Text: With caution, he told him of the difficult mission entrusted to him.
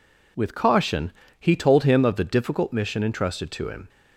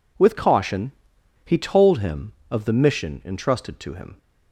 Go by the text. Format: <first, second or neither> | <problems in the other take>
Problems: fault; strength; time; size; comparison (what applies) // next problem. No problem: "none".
first | skips "difficult"; at 2.7 s